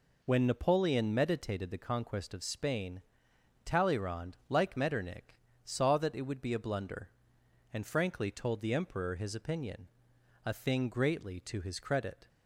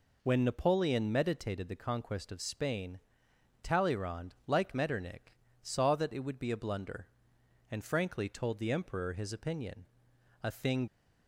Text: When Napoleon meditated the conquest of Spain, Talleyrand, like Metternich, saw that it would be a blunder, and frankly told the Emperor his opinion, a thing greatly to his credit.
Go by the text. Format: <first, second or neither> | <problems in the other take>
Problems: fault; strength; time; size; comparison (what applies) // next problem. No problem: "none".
first | stops before "greatly to his credit"; at 10.8 s